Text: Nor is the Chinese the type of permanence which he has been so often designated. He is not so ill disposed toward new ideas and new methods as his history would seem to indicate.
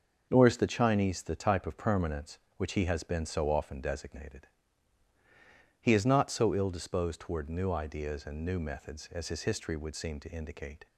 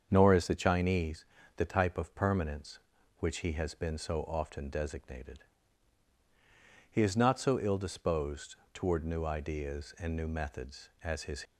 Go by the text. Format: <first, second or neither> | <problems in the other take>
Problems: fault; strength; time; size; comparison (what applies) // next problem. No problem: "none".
first | starts louder than the rest; strong; until 1.1 s; 7 dB; noticeable in the first // pauses between "Chinese" and "the"; slight; at 1.2 s; 0.32 s long // pauses between "disposed" and "toward"; slight; at 8.5 s; 0.18 s long // stops before "history would seem to indicate"; at 11.4 s